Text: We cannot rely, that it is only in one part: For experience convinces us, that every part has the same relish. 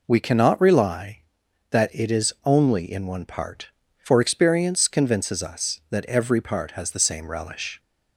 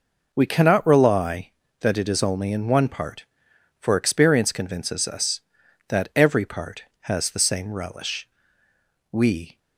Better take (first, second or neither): first